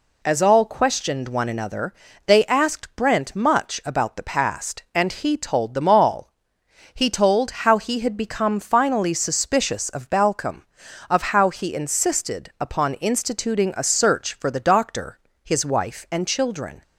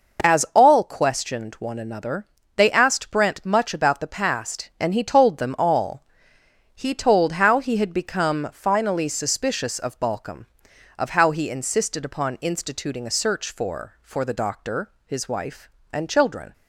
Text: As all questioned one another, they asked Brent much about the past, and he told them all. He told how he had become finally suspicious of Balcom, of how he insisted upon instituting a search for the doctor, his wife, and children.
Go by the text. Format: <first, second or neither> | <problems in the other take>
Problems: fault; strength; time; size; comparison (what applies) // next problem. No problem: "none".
first | says "for" twice; at 14.0 s